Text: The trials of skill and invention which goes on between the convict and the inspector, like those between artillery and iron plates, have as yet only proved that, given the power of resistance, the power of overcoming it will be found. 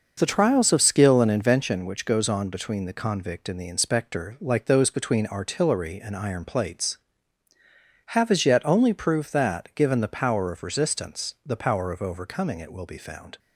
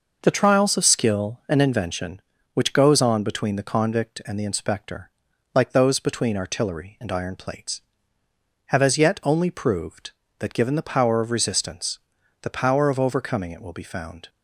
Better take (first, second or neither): neither